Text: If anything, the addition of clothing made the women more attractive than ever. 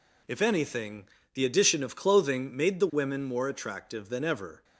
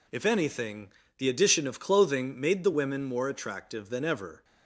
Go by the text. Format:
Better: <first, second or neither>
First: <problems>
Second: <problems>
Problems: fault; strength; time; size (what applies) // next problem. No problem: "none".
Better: neither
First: none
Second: none